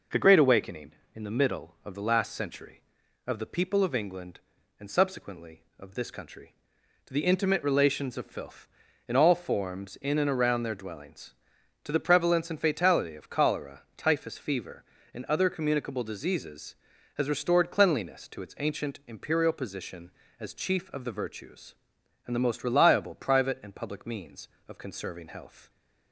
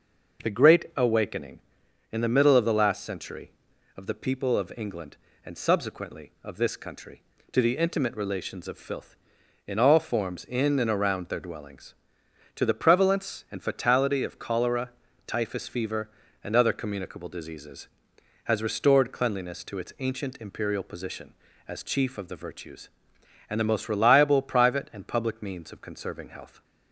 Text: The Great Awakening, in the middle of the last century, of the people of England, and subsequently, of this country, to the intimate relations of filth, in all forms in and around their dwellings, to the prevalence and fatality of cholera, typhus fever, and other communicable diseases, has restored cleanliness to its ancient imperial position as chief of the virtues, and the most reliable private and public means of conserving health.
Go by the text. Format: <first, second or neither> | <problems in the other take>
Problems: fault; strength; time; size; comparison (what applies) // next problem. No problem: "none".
neither | none